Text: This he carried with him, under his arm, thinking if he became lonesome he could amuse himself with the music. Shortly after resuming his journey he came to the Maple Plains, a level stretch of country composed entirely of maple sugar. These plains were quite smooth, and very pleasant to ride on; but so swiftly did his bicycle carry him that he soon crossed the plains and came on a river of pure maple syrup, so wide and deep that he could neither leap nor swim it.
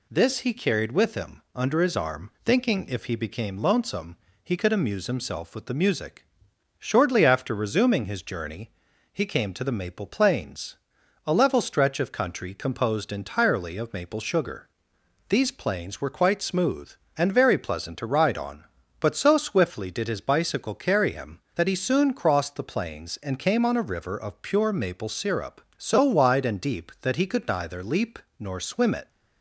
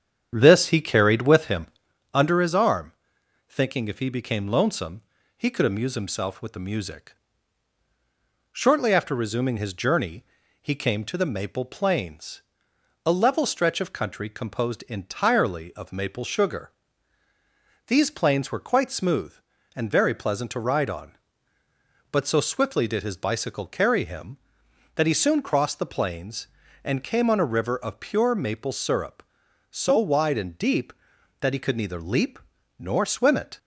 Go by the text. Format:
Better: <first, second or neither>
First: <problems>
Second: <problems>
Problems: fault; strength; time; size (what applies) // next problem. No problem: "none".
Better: first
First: pauses between "lonesome" and "he"; slight; at 4.1 s; 0.26 s long // pauses between "journey" and "he"; at 8.7 s; 0.42 s long // pauses between "leap" and "nor"; slight; at 28.1 s; 0.20 s long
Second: starts louder than the rest; strong; until 2.0 s; 8.5 dB // pauses between "lonesome" and "he"; slight; at 5.0 s; 0.34 s long // pauses between "journey" and "he"; slight; at 10.2 s; 0.36 s long // pauses between "leap" and "nor"; at 32.3 s; 0.40 s long